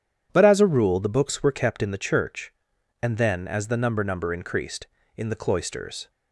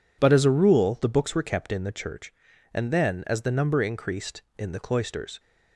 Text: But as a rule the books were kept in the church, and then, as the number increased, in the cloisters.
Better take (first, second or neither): second